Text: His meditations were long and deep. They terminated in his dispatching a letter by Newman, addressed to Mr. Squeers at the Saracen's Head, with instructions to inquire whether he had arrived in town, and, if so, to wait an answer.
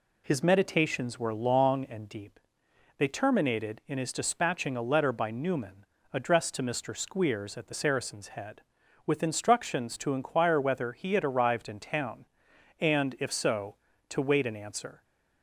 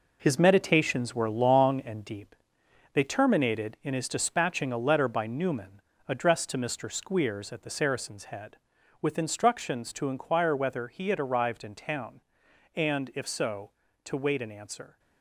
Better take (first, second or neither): first